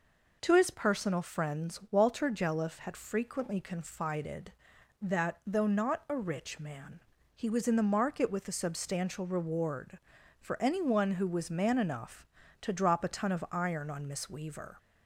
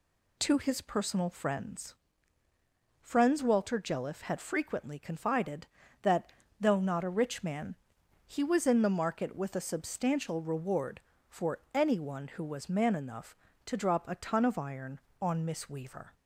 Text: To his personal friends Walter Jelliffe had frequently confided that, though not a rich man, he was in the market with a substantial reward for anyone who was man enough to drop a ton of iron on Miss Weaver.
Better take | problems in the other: first | says "friends" twice; at 3.0 s

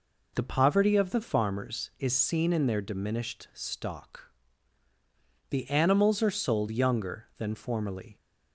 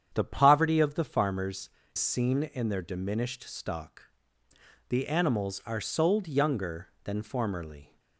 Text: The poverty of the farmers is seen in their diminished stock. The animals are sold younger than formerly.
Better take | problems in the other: first | starts louder than the rest; strong; until 1.1 s; 8.5 dB // skips "is"; at 1.8 s

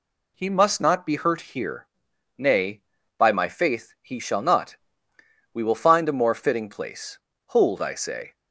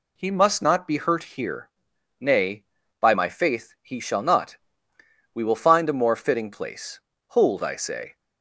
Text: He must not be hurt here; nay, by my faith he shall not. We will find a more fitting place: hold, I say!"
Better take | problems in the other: neither | none

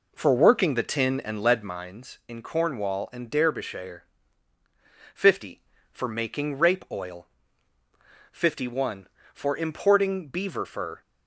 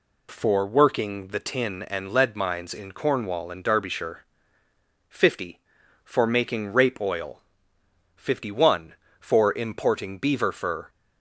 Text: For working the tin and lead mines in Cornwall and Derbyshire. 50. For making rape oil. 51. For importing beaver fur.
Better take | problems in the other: second | starts louder than the rest; noticeable; until 1.7 s; 4 dB

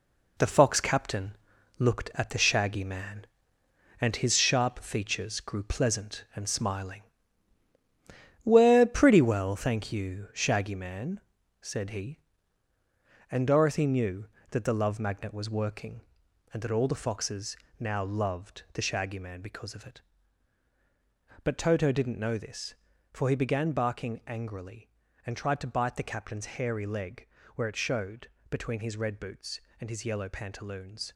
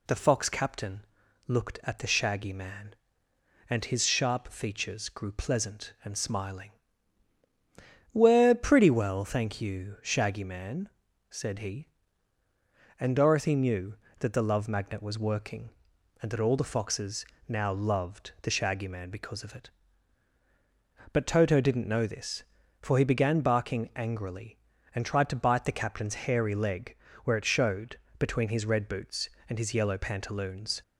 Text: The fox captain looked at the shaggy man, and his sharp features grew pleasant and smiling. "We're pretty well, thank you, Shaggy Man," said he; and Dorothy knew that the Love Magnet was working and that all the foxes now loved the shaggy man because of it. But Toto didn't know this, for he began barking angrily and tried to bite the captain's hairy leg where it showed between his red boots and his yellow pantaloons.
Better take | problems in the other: second | gets quieter; strong; throughout; 8 dB // pauses between "captain" and "looked"; noticeable; at 1.3 s; 0.46 s long; noticeable in the second // pauses between "foxes" and "now"; slight; at 17.5 s; 0.22 s long; slight in the second // pauses between "leg" and "where"; slight; at 27.2 s; 0.28 s long; slight in the second // pauses between "showed" and "between"; slight; at 28.2 s; 0.20 s long; slight in the second

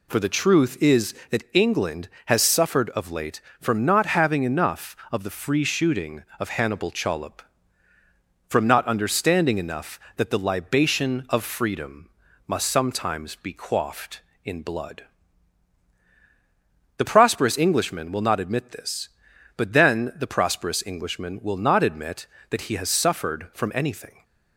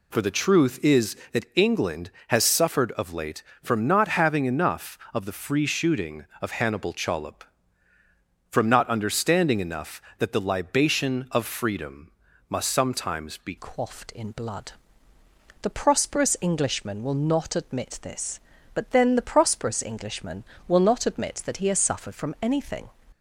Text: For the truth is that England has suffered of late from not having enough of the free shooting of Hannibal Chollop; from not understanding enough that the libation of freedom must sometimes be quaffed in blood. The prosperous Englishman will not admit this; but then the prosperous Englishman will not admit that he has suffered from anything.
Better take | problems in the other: first | pauses between "freedom" and "must"; at 12.1 s; 0.38 s long; also in the first // changes voice at "quaffed"; from 13.5 s on; 9.4 s long

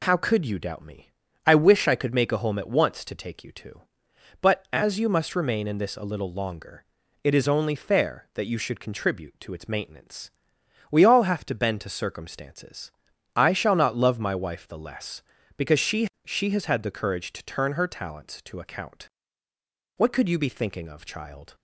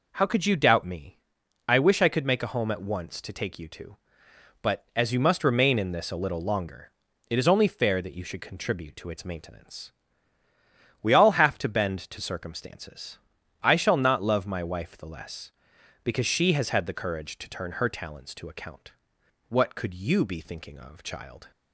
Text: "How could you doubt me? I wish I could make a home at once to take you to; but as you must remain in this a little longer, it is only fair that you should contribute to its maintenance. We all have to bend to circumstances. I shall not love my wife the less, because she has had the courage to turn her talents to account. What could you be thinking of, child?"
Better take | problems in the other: second | says "she" twice; at 16.2 s

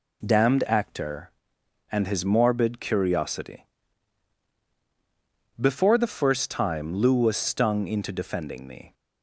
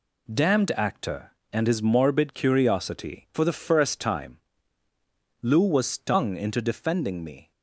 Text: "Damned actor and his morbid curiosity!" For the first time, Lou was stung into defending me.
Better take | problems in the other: second | says "Before" for "For"; at 5.5 s

